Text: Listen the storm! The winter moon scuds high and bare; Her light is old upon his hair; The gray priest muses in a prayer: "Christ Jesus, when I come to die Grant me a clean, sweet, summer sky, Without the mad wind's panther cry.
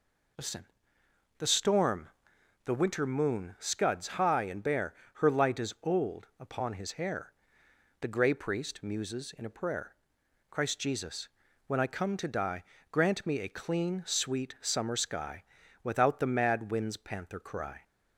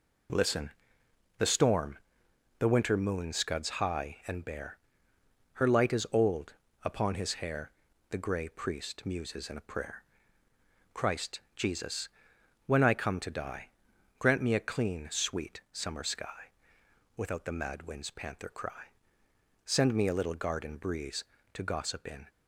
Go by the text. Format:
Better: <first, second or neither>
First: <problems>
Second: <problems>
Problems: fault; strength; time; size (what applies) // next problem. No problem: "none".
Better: first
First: pauses between "Listen" and "the"; noticeable; at 0.6 s; 0.74 s long // pauses between "die" and "Grant"; slight; at 12.6 s; 0.28 s long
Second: pauses between "Listen" and "the"; noticeable; at 0.7 s; 0.68 s long // pauses between "old" and "upon"; slight; at 6.5 s; 0.32 s long // pauses between "Christ" and "Jesus"; slight; at 11.4 s; 0.16 s long // pauses between "die" and "Grant"; noticeable; at 13.7 s; 0.48 s long // goes on to say "Send me a little garden breeze To gossip in"; strong; from 19.6 s on; 2.6 s long